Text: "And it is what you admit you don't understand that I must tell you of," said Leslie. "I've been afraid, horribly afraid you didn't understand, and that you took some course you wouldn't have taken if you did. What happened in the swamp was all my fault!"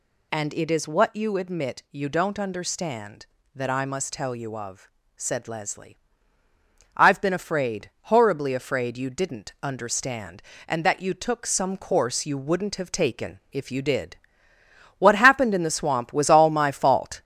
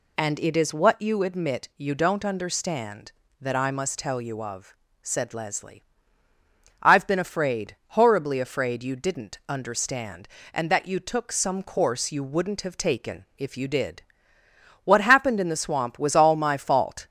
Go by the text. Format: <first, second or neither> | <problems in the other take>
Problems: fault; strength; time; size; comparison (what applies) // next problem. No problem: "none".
second | gets louder; throughout; 4 dB